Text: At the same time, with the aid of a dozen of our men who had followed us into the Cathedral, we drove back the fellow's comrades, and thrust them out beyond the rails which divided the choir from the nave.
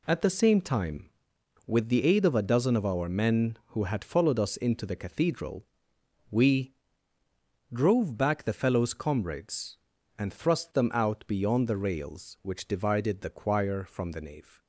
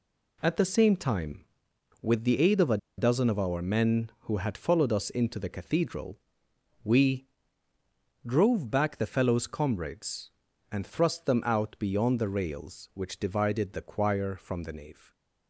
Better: first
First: pauses between "we" and "drove"; noticeable; at 6.7 s; 0.98 s long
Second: pauses between "a" and "dozen"; slight; at 2.7 s; 0.20 s long // pauses between "we" and "drove"; noticeable; at 7.2 s; 0.98 s long

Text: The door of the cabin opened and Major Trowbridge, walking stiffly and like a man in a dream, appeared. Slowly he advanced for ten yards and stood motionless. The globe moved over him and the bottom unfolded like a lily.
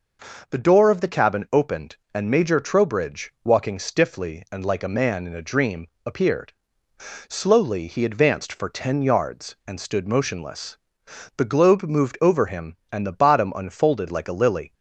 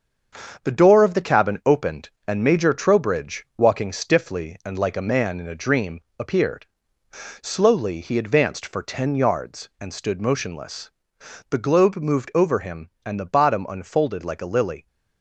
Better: first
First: none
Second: gets quieter; noticeable; throughout; 5.5 dB

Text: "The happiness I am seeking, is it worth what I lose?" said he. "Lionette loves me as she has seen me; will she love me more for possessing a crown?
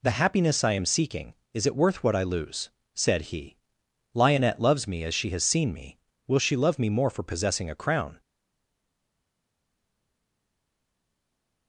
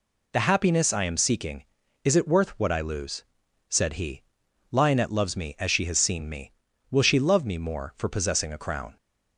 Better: second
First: stays silent after the last word; strong; from 8.1 s on; 3.5 s long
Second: none

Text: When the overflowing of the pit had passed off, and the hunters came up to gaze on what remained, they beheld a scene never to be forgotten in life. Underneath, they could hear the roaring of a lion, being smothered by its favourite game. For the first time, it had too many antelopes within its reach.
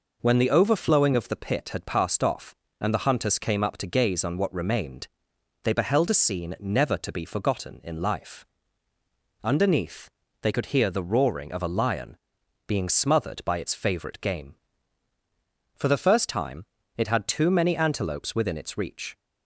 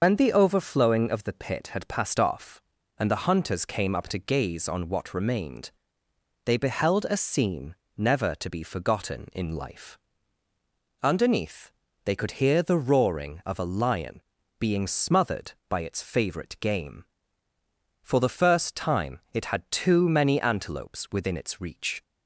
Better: first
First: none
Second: loses the start of "When"; at 0.0 s; 100 ms // starts louder than the rest; until 1.0 s; 6 dB // pauses between "scene" and "never"; slight; at 7.7 s; 0.20 s long

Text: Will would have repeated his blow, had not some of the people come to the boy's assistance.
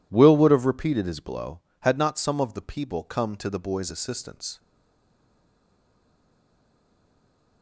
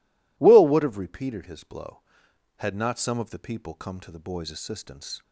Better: second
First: stays silent after the last word; strong; from 4.5 s on; 3.1 s long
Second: none

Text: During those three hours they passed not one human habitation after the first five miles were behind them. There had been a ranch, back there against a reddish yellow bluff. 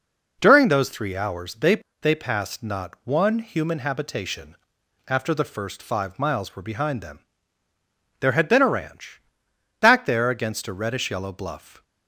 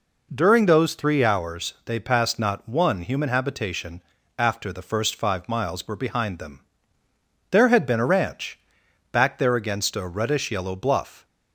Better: second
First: says "they" twice; at 2.0 s // pauses between "habitation" and "after"; noticeable; at 4.5 s; 0.54 s long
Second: pauses between "habitation" and "after"; at 3.9 s; 0.38 s long

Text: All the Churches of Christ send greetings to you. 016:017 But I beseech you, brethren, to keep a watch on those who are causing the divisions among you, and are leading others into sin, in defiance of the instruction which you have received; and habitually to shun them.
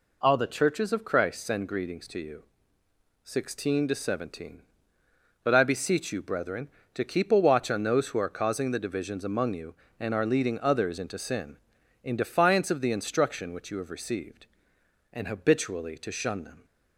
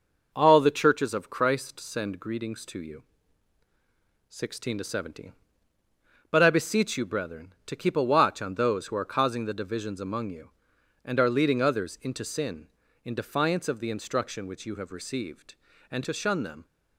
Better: first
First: none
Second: skips "habitually"; at 16.0 s

